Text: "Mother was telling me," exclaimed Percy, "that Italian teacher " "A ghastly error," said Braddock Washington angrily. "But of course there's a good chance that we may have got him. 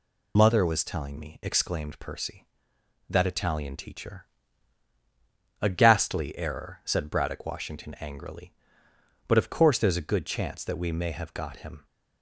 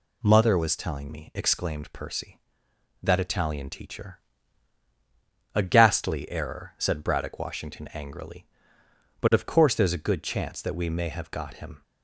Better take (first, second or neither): second